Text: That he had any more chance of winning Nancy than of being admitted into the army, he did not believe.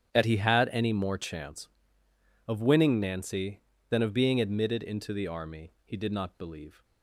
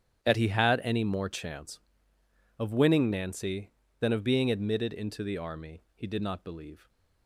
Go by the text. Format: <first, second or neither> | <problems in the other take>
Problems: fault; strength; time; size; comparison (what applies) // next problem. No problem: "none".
neither | starts louder than the rest; strong; the same in both